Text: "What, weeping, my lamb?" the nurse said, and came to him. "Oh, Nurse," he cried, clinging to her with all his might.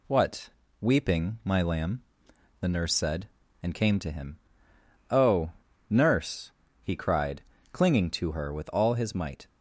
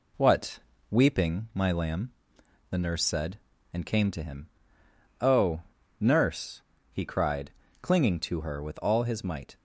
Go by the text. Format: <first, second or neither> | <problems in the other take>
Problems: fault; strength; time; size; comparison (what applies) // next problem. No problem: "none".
first | starts louder than the rest; slight; until 1.2 s; 2.5 dB